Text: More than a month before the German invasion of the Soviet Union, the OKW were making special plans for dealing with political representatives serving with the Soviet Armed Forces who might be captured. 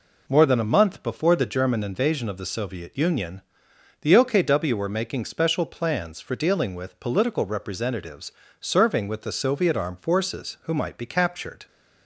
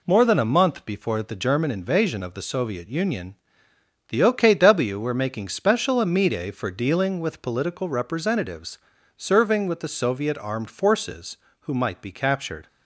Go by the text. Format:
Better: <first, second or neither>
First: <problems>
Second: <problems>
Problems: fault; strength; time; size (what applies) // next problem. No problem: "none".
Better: first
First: pauses between "representatives" and "serving"; slight; at 8.3 s; 0.28 s long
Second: says "amide" for "plans"; at 5.9 s // pauses between "representatives" and "serving"; slight; at 8.7 s; 0.36 s long